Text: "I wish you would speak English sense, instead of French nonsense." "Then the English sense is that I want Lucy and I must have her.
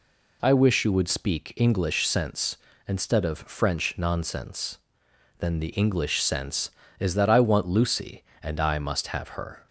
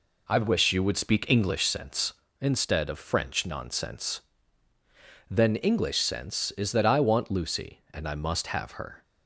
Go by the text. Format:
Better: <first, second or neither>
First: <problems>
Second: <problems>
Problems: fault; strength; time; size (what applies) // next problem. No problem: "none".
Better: first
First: none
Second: skips "the"; at 5.5 s